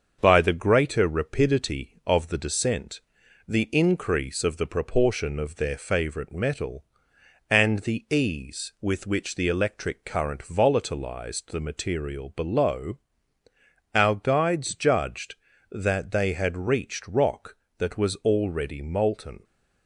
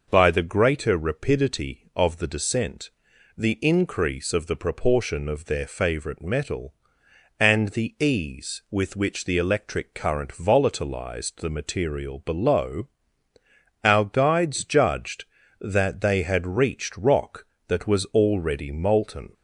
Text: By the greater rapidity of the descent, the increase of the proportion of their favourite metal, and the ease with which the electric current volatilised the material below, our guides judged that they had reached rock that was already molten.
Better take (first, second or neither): second